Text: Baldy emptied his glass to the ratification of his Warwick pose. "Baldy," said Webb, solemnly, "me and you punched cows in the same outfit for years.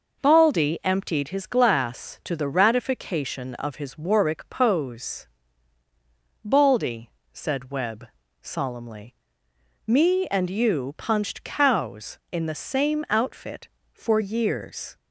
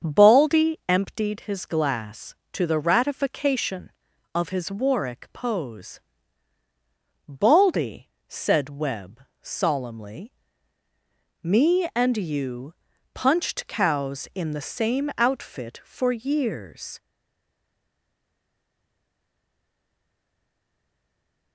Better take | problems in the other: first | starts louder than the rest; until 1.1 s; 7 dB // pauses between "you" and "punched"; at 12.7 s; 0.40 s long // stays silent after the last word; strong; from 16.9 s on; 4.6 s long

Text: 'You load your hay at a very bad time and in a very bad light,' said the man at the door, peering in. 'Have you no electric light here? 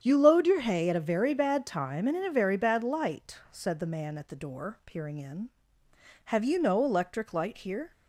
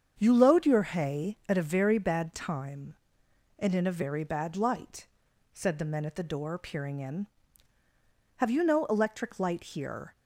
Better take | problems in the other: first | starts louder than the rest; strong; until 1.2 s; 7.5 dB; strong in the first // says "men" for "man"; at 5.8 s

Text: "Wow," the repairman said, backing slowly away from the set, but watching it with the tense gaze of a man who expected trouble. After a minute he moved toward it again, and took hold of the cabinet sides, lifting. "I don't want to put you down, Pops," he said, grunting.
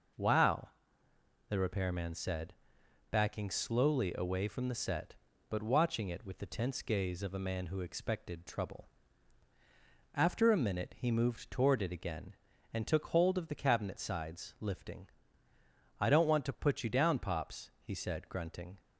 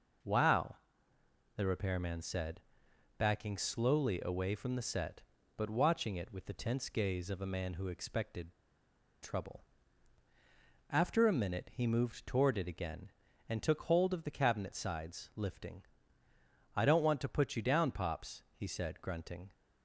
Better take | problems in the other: first | pauses between "expected" and "trouble"; noticeable; at 8.5 s; 0.70 s long

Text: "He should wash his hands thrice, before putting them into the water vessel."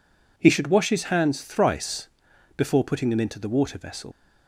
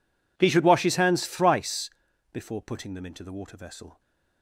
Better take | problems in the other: second | leaves "vessel" unfinished; at 4.1 s; 105 ms

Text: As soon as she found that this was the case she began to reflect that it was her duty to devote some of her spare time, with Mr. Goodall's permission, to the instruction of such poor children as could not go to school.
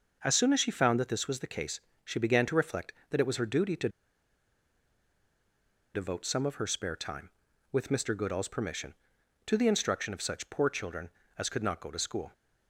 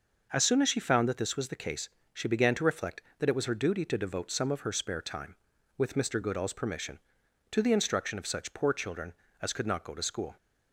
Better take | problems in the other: second | pauses between "case" and "she"; slight; at 1.8 s; 0.24 s long; slight in the second // pauses between "to" and "devote"; strong; at 3.8 s; 2.0 s long

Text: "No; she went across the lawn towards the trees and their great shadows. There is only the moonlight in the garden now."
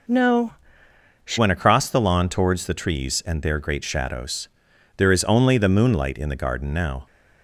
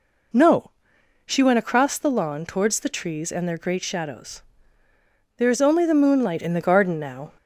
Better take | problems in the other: second | changes voice at "went"; from 1.3 s on; 5.7 s long

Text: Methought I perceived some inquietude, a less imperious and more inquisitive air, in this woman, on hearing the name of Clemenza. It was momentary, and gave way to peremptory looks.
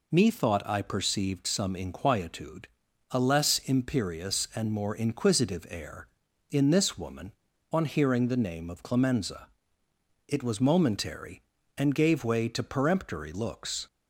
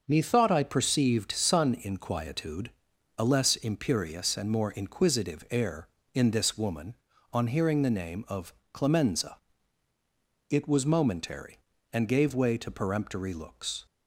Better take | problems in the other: first | starts louder than the rest; noticeable; until 1.0 s; 6 dB // says "sun" for "some"; at 1.3 s // pauses between "of" and "Clemenza"; slight; at 8.5 s; 0.22 s long

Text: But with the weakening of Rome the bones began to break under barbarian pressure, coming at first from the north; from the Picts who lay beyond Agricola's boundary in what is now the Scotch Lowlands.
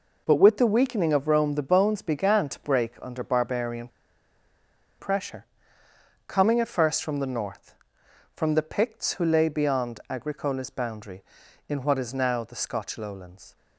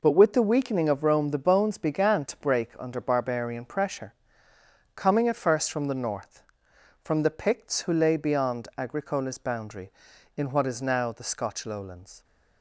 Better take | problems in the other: second | pauses between "barbarian" and "pressure"; at 3.8 s; 1.1 s long

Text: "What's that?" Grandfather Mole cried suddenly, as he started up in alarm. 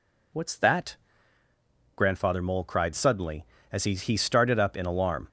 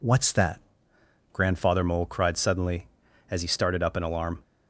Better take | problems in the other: second | says "he" twice; at 3.9 s

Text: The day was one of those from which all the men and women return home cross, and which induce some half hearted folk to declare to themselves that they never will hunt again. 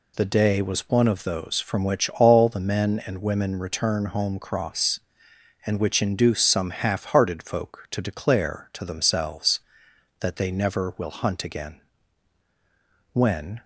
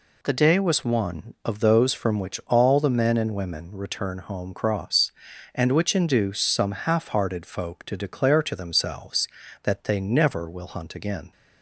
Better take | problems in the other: second | goes on to say "When"; from 13.1 s on; 0.50 s long

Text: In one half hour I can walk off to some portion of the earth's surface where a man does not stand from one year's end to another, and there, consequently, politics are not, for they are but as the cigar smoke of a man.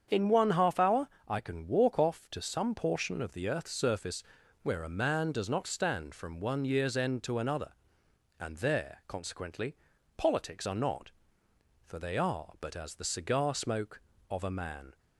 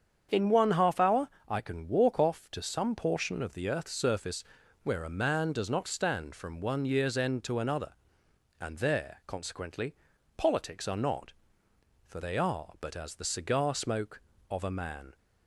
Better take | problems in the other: neither | starts louder than the rest; strong; the same in both // pauses between "hour" and "I"; slight; the same in both // pauses between "surface" and "where"; the same in both

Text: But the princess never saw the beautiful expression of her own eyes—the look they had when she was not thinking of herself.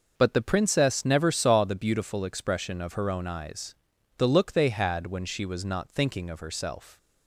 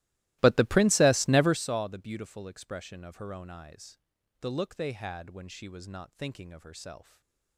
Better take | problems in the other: first | starts louder than the rest; strong; until 1.7 s; 18 dB // stays silent after the last word; slight; from 7.0 s on; 0.5 s long

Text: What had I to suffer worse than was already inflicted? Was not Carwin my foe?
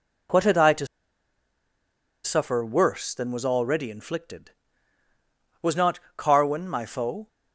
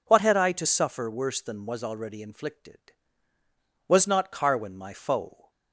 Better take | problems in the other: second | pauses between "to" and "suffer"; strong; at 0.8 s; 1.3 s long // pauses between "not" and "Carwin"; slight; at 5.9 s; 0.16 s long

